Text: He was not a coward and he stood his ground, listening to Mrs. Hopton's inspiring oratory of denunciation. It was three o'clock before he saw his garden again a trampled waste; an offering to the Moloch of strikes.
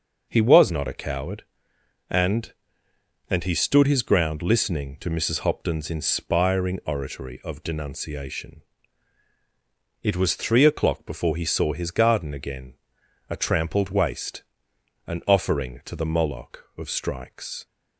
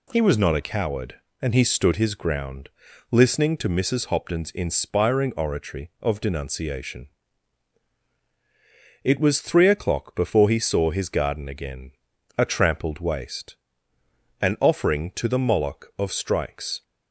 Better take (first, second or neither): second